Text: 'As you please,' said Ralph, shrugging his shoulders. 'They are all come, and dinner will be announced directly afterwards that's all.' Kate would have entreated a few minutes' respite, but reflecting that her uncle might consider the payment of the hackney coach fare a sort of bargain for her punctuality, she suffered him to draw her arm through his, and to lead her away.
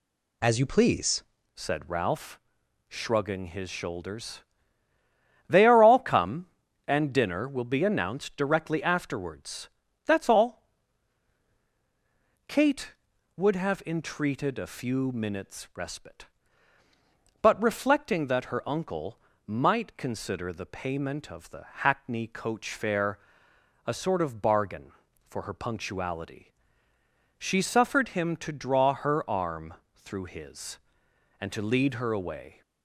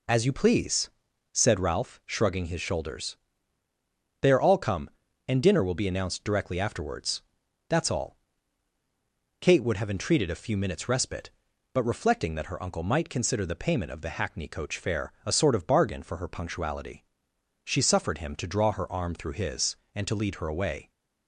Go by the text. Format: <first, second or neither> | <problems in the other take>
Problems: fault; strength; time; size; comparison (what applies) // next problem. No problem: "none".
second | changes voice at "said"; from 1.5 s on; 31.1 s long // pauses between "afterwards" and "that's"; at 9.6 s; 0.38 s long; noticeable in the second // pauses between "uncle" and "might"; slight; at 19.1 s; 0.26 s long // pauses between "the" and "hackney"; slight; at 21.6 s; 0.18 s long // pauses between "fare" and "a"; noticeable; at 23.1 s; 0.66 s long // pauses between "arm" and "through"; slight; at 29.7 s; 0.20 s long